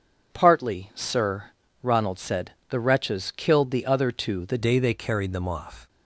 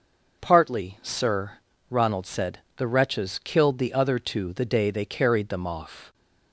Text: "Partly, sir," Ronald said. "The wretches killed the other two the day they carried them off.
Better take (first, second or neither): second